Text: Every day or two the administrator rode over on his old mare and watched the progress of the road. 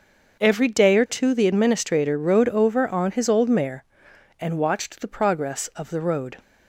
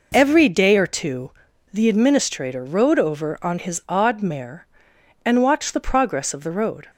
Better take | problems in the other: first | pauses between "two" and "the"; at 1.3 s; 0.42 s long // says "odd" for "old"; at 3.8 s

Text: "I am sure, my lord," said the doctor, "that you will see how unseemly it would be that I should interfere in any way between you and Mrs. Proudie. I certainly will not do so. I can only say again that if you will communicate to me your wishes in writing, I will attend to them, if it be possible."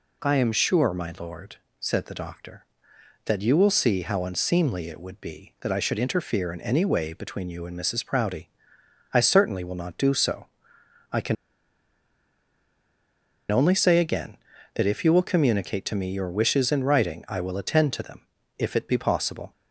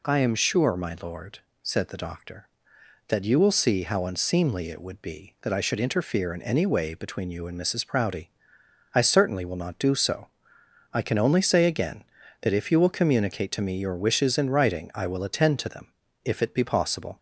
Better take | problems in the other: second | pauses between "can" and "only"; strong; at 11.3 s; 2.1 s long

